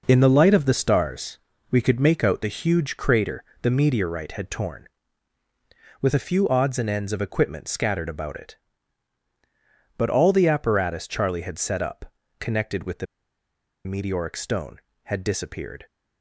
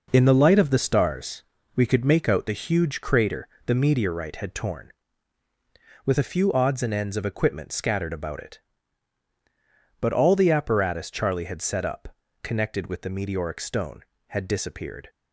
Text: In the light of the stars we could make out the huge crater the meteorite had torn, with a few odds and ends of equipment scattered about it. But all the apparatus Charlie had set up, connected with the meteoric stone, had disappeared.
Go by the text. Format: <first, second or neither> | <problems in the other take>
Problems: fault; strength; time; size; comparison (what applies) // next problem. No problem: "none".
second | pauses between "stars" and "we"; slight; at 1.3 s; 0.32 s long; slight in the second // pauses between "crater" and "the"; slight; at 3.4 s; 0.20 s long; slight in the second // pauses between "the" and "meteoric"; noticeable; at 13.0 s; 0.80 s long